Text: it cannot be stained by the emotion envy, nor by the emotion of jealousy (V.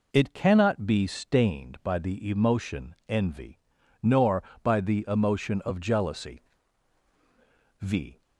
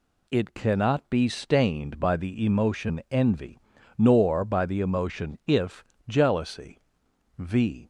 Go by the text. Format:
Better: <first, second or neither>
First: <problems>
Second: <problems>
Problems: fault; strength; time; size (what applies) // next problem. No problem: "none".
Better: first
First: none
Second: says "if" for "of"; at 5.4 s